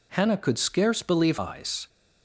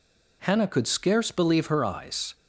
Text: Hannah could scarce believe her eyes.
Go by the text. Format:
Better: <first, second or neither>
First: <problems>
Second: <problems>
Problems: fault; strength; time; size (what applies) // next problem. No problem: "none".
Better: second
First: skips "her"; at 1.3 s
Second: none